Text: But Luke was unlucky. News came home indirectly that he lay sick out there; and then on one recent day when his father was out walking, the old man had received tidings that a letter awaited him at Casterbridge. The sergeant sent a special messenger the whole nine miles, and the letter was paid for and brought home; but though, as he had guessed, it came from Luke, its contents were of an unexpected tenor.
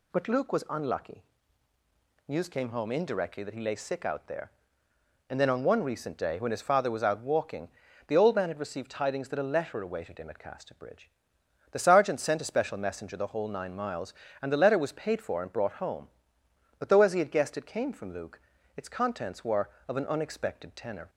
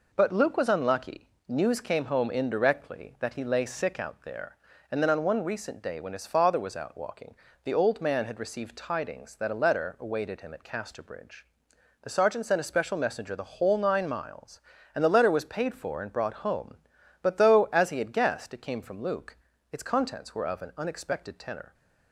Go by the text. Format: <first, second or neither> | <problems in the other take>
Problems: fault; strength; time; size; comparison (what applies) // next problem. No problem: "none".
neither | none